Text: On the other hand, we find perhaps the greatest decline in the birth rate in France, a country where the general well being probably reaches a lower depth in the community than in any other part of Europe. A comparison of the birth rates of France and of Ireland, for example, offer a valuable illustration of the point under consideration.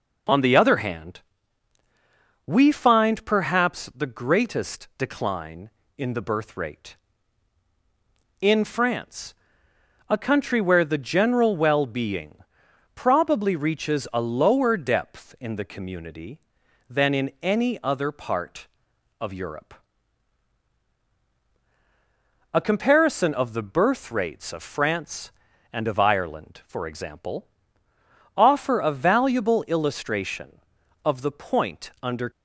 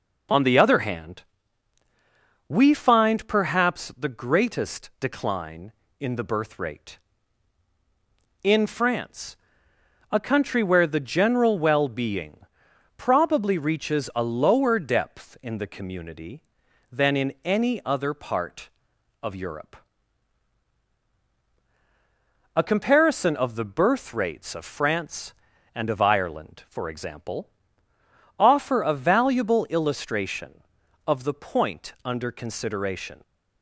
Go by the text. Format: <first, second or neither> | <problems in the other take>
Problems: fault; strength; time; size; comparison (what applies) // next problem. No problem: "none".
second | pauses between "being" and "probably"; noticeable; at 12.3 s; 0.58 s long; noticeable in the second // stops before "consideration"; at 32.3 s